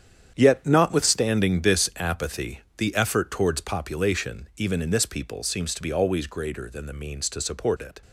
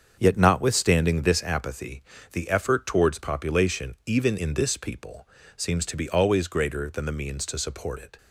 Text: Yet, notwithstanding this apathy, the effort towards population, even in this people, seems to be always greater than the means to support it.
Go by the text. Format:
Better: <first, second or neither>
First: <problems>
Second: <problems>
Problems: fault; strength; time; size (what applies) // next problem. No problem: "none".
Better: second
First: gets quieter; strong; throughout; 10.5 dB // starts louder than the rest; strong; until 1.3 s; 8.5 dB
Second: starts louder than the rest; until 1.1 s; 7 dB